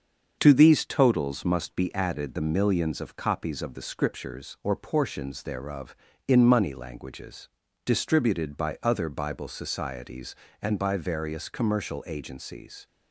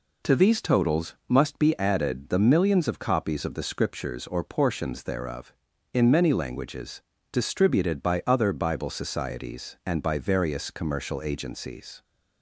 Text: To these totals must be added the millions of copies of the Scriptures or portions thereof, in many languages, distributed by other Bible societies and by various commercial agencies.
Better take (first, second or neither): second